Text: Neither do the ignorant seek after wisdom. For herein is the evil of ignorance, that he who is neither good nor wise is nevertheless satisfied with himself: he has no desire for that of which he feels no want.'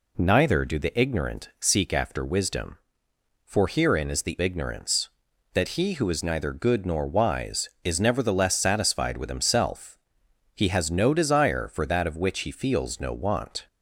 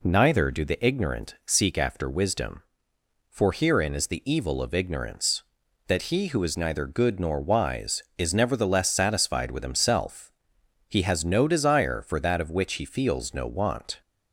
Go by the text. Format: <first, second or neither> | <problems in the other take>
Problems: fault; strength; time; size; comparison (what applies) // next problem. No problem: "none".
second | skips "evil of"; at 4.3 s